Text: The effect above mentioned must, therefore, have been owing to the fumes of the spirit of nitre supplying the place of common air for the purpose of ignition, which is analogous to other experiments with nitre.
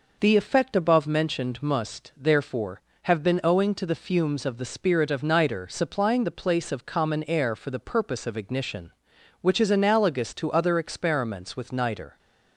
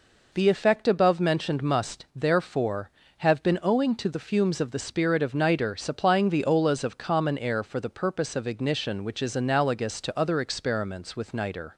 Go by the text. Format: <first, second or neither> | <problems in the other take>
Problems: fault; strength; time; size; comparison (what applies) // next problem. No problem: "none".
first | says "olas" for "place"; at 6.4 s